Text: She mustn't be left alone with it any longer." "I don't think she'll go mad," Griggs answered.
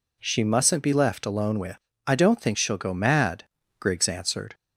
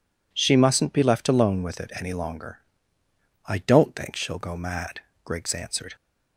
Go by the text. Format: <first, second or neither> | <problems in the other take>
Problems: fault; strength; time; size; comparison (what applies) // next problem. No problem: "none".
second | skips "it any longer"; at 1.9 s